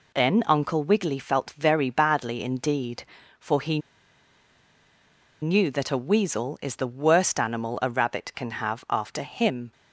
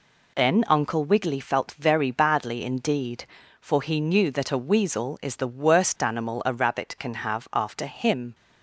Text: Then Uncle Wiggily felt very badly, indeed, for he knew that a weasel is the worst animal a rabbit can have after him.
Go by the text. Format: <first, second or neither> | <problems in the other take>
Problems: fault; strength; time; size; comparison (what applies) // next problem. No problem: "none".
second | pauses between "he" and "knew"; strong; at 3.7 s; 1.6 s long